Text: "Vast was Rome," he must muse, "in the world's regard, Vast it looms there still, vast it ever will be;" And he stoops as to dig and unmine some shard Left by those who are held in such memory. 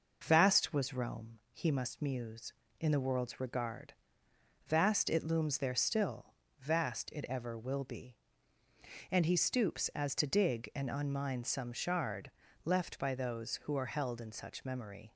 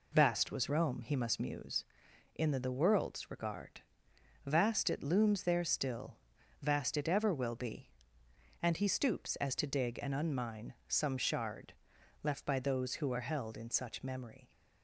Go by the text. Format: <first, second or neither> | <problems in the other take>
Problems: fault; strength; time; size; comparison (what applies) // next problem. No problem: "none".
first | says "the" twice; at 2.5 s // pauses between "shard" and "Left"; noticeable; at 11.7 s; 0.48 s long; slight in the first